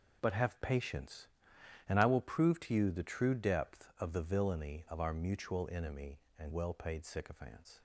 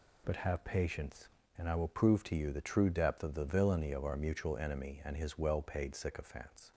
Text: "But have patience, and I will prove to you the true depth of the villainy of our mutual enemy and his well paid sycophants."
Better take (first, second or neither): second